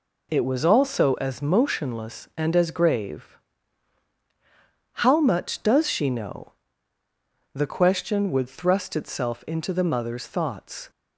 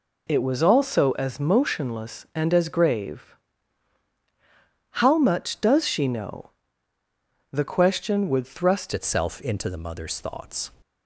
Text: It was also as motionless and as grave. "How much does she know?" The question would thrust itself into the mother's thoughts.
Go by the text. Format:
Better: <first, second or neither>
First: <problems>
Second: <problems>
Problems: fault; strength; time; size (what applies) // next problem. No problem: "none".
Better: first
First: none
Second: changes voice at "itself"; from 8.9 s on; 1.8 s long